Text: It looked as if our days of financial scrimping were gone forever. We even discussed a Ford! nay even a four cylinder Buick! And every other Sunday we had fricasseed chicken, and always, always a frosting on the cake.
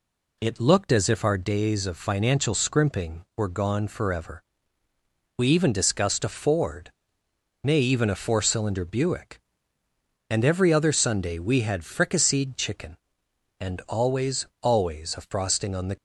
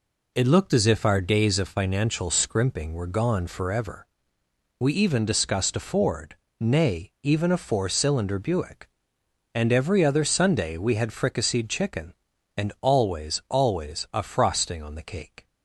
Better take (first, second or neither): second